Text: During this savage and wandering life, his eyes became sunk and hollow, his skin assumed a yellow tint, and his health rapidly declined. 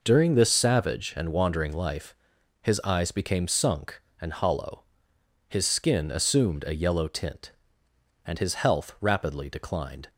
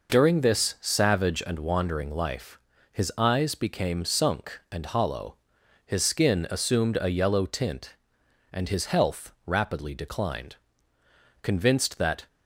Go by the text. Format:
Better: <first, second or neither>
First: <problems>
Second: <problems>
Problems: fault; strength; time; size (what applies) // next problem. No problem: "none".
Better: first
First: none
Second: pauses between "health" and "rapidly"; slight; at 9.3 s; 0.16 s long // goes on to say "Convinced that"; noticeable; from 11.4 s on; 0.86 s long